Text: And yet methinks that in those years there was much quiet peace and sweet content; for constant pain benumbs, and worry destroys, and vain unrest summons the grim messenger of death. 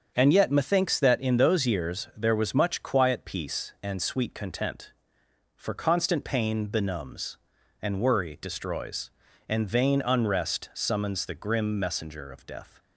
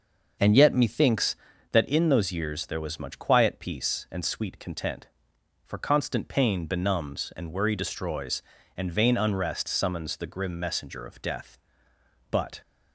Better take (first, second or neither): first